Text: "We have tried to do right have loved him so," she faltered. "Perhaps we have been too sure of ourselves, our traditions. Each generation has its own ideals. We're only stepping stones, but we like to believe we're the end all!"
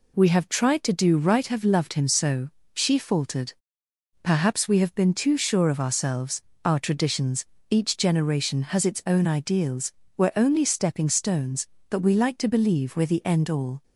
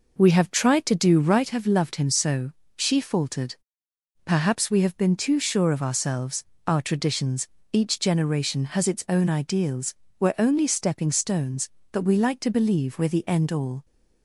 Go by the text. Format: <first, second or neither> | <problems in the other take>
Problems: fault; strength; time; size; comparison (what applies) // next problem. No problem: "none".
first | starts louder than the rest; noticeable; until 1.4 s; 5 dB